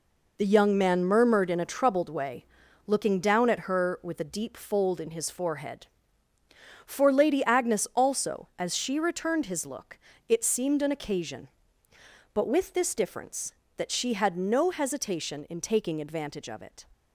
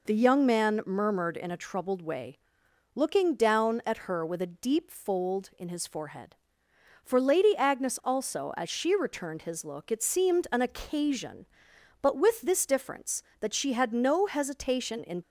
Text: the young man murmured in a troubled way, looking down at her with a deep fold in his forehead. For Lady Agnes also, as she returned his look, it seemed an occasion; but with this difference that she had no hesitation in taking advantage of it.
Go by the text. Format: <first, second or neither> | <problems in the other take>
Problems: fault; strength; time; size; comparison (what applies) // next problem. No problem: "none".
first | stops before "taking advantage of it"; at 15.2 s